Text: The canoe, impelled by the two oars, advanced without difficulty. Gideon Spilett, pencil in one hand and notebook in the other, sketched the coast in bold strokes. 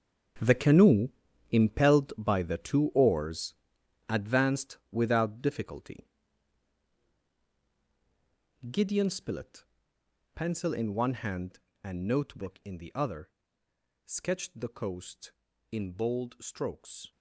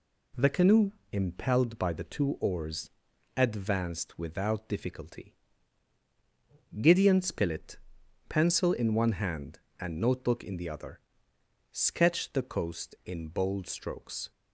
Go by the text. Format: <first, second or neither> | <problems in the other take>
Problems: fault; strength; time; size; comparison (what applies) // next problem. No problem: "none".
second | gets quieter; strong; throughout; 13 dB